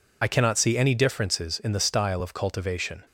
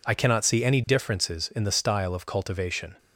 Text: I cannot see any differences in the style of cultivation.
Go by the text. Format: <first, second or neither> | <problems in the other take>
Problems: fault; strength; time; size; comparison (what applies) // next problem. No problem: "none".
second | loses the start of "I"; at 0.2 s; 45 ms